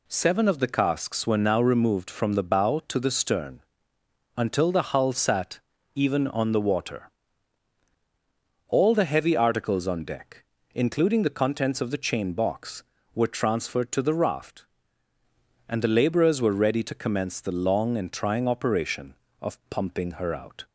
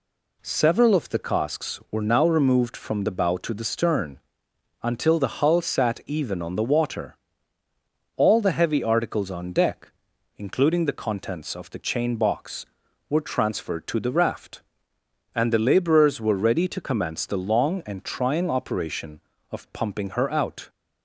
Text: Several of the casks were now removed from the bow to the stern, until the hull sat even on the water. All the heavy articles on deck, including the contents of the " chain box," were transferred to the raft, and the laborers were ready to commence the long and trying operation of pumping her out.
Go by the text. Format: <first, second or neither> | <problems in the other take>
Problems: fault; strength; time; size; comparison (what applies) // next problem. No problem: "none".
second | says "Seven" for "Several"; at 0.0 s // pauses between "sat" and "even"; at 5.5 s; 0.38 s long